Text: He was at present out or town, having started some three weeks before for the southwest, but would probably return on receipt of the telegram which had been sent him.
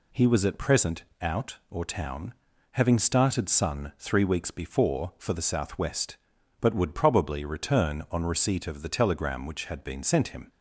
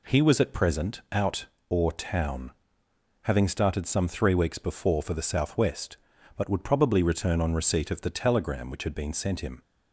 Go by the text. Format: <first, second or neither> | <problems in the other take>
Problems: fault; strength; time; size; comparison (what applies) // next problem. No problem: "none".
second | pauses between "present" and "out"; slight; at 1.0 s; 0.18 s long // says "sun" for "some"; at 3.4 s